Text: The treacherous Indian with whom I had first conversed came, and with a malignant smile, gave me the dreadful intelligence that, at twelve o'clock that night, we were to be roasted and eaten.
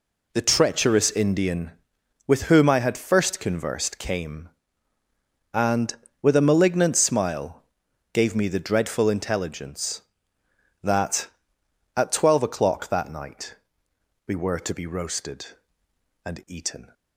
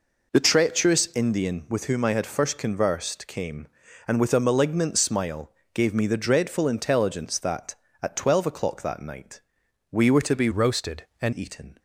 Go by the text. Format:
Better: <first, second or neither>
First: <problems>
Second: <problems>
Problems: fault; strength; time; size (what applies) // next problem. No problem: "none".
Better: first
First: none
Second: changes voice from "roasted" to "and"; from 10.5 to 11.3 s; 0.8 s long